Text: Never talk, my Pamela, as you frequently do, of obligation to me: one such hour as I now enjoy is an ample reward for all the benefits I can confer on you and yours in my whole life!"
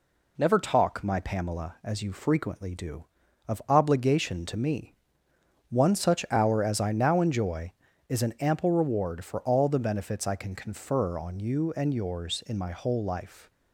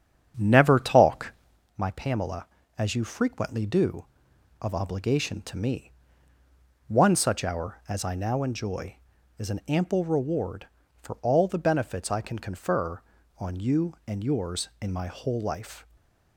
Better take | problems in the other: first | starts louder than the rest; strong; until 1.7 s; 8.5 dB // stays silent after the last word; slight; from 15.8 s on; 0.5 s long

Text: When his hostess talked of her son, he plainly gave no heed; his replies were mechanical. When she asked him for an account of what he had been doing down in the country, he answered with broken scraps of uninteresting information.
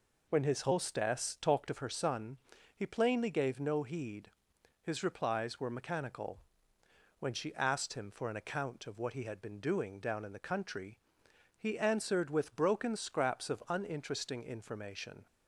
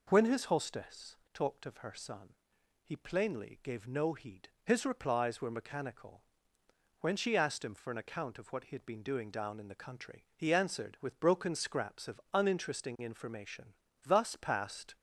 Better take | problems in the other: first | pauses between "hostess" and "talked"; slight; at 1.1 s; 0.18 s long // goes on to say "Thus passed"; noticeable; from 14.0 s on; 0.90 s long

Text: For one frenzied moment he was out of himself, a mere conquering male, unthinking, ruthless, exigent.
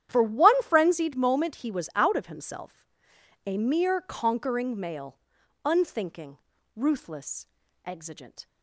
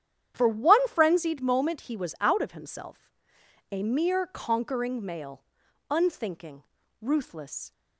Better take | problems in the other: first | starts louder than the rest; strong; until 1.3 s; 10 dB; strong in the first // stops before "exigent"; at 7.7 s

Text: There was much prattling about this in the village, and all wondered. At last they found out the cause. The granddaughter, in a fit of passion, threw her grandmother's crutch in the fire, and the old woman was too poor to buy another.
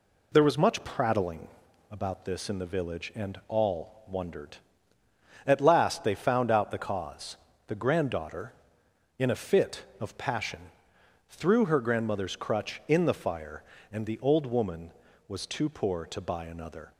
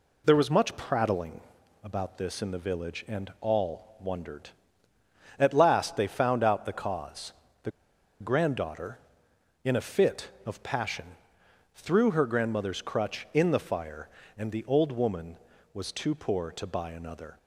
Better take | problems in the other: first | pauses between "prattling" and "about"; at 1.3 s; 0.44 s long; also in the first // pauses between "The" and "granddaughter"; noticeable; at 7.6 s; 0.51 s long

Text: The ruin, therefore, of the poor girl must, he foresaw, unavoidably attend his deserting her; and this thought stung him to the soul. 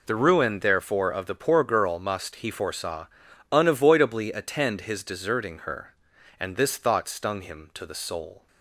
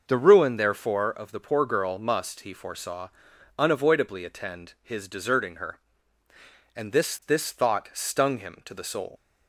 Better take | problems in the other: first | says "this" twice; at 7.2 s

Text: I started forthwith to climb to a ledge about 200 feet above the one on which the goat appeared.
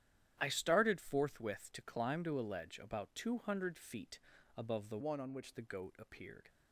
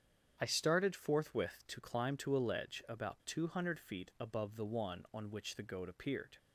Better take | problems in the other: second | starts louder than the rest; strong; until 1.4 s; 11 dB; strong in the second // pauses between "feet" and "above"; slight; at 4.2 s; 0.36 s long // changes voice from "one" to "which"; from 4.9 to 5.5 s; 0.6 s long

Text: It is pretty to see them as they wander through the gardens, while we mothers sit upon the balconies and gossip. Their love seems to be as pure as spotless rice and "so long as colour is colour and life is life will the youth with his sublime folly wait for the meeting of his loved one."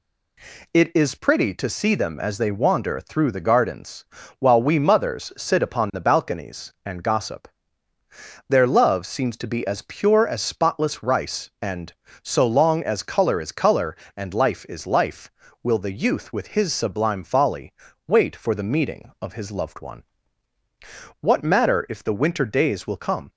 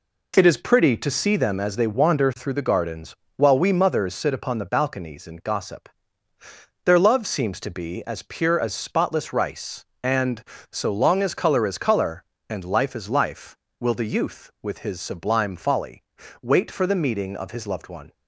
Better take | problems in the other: second | pauses between "folly" and "wait"; slight; at 17.7 s; 0.36 s long; also in the second // goes on to say "What matter if the winter days will come"; strong; from 21.1 s on; 2.1 s long

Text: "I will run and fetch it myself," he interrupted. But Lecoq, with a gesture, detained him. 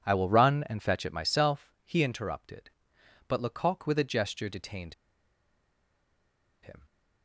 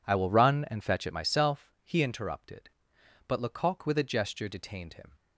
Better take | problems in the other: second | pauses between "detained" and "him"; strong; at 4.9 s; 1.6 s long

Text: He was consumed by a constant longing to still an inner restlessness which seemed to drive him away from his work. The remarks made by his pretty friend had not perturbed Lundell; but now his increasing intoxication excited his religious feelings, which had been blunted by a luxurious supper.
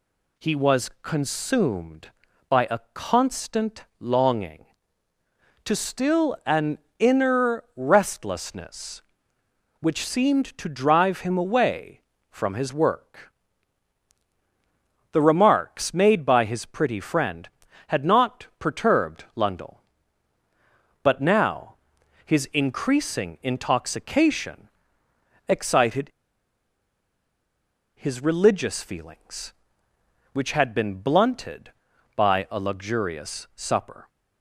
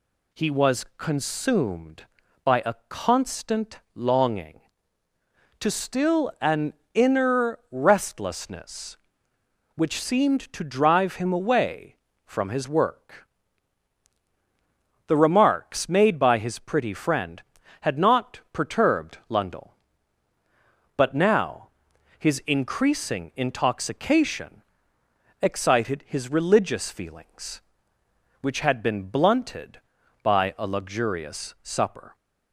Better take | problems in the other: second | pauses between "an" and "inner"; slight; at 6.7 s; 0.20 s long; slight in the second // pauses between "now" and "his"; noticeable; at 21.7 s; 0.48 s long; noticeable in the second // pauses between "intoxication" and "excited"; noticeable; at 24.6 s; 0.80 s long; noticeable in the second // pauses between "excited" and "his"; strong; at 26.1 s; 1.8 s long

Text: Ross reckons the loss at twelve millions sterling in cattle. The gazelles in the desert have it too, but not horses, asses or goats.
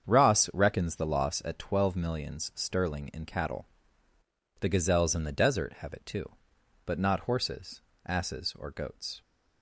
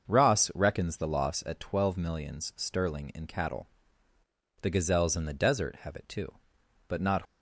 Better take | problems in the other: first | starts louder than the rest; noticeable; until 1.1 s; 6 dB; strong in the first // stops before "horses asses or goats"; at 7.2 s

